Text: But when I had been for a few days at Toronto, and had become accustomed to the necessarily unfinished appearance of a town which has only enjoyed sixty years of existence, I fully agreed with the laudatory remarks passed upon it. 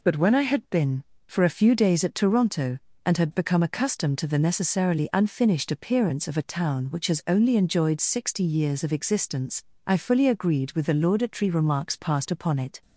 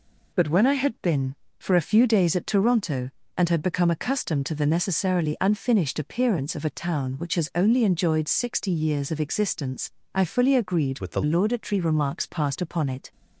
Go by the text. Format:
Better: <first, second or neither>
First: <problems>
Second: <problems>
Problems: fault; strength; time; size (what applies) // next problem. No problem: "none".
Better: first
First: none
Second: changes voice from "with" to "the"; from 10.9 to 11.2 s; 0.3 s long